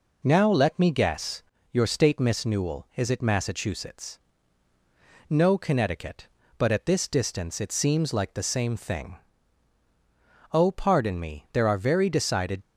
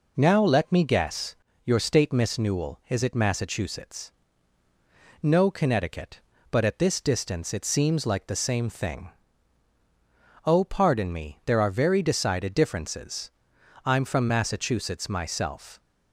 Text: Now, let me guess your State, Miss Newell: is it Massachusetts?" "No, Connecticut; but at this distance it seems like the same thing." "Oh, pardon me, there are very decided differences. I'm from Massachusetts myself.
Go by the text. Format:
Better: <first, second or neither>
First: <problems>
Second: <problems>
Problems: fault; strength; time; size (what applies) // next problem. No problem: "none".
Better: second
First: pauses between "guess" and "your"; slight; at 1.4 s; 0.30 s long // stops before "differences I'm from Massachusetts myself"; at 12.6 s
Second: pauses between "guess" and "your"; slight; at 1.3 s; 0.30 s long